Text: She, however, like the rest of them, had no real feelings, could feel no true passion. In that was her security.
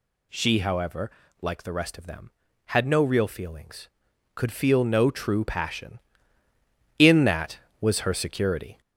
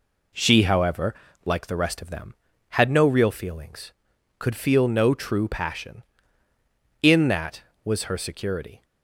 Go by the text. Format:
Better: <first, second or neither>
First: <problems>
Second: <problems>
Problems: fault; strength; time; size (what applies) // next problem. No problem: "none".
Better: second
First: gets louder; slight; throughout; 3 dB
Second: none